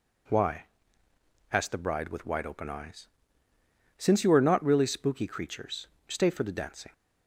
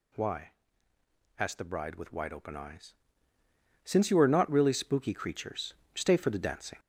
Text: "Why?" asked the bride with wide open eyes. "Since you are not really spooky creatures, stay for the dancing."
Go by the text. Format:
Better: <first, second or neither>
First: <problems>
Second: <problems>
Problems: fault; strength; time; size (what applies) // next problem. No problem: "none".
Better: first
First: none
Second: gets louder; noticeable; throughout; 5 dB